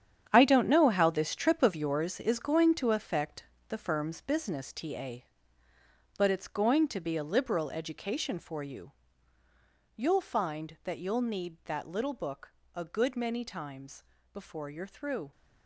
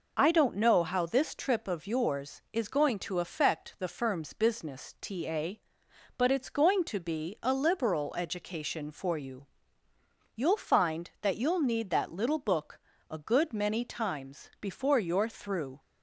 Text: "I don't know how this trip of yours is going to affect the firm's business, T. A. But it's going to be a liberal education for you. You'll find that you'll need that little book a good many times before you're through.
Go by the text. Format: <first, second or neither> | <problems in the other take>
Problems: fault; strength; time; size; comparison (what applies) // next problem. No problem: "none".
second | gets quieter; strong; throughout; 11.5 dB // pauses between "affect" and "the"; slight; at 3.4 s; 0.24 s long // pauses between "book" and "a"; slight; at 12.5 s; 0.24 s long; slight in the second // pauses between "times" and "before"; slight; at 14.0 s; 0.30 s long